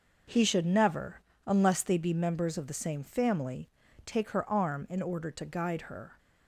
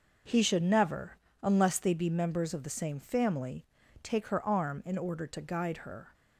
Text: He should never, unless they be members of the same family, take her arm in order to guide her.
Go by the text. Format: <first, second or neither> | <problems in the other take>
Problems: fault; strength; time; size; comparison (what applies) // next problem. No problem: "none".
neither | none